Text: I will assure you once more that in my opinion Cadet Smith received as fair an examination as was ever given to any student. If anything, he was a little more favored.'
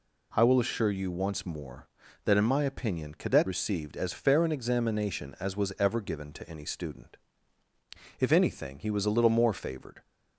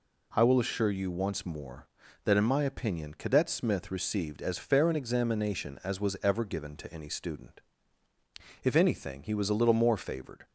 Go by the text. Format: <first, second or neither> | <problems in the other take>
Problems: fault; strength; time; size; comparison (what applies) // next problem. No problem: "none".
second | skips "Smith"; at 3.4 s